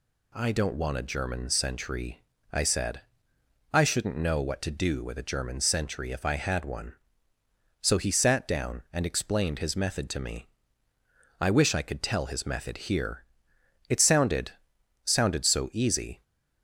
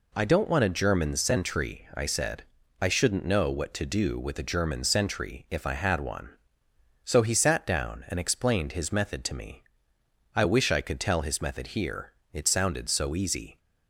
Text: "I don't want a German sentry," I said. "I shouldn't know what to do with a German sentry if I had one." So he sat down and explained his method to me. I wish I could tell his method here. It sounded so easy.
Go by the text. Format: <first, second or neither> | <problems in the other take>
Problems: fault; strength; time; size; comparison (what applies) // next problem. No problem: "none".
second | says "sounded" twice; at 15.0 s